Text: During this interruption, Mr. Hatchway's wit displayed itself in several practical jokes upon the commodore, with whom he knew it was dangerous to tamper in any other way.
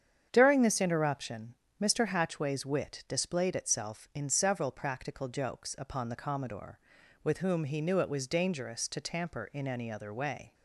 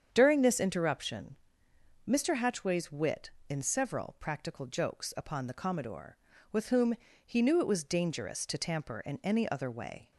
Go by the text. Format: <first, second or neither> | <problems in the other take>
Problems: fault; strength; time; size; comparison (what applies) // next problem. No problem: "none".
first | starts louder than the rest; strong; until 1.1 s; 8 dB; strong in the first // skips "displayed itself"; at 3.3 s // pauses between "whom" and "he"; slight; at 6.9 s; 0.30 s long